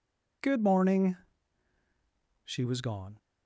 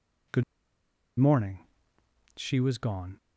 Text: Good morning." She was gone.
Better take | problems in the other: first | pauses between "Good" and "morning"; noticeable; at 0.4 s; 0.74 s long

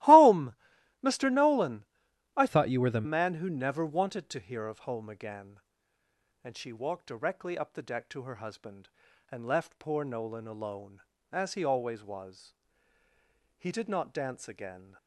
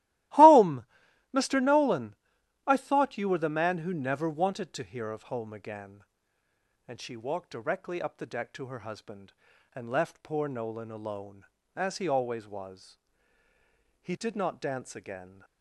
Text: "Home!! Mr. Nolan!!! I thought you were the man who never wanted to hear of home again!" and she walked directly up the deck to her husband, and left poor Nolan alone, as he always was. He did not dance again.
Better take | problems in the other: second | starts louder than the rest; strong; until 1.5 s; 17.5 dB; strong in the second // changes voice from "thought" to "the"; from 2.4 to 3.0 s; 0.6 s long

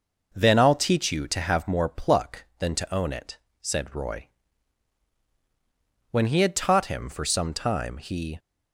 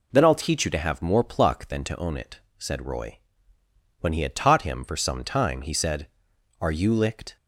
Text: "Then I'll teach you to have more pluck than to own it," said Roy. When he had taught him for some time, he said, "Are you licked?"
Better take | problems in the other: second | stops before "said Are you licked"; at 8.3 s

